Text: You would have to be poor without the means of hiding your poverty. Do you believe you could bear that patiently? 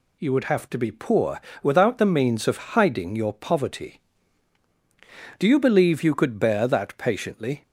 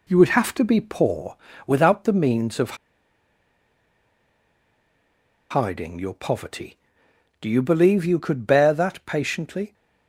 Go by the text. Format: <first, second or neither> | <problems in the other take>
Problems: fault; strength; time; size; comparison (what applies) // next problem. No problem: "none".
first | pauses between "poor" and "without"; slight; at 1.3 s; 0.30 s long; slight in the first // pauses between "of" and "hiding"; strong; at 2.7 s; 2.7 s long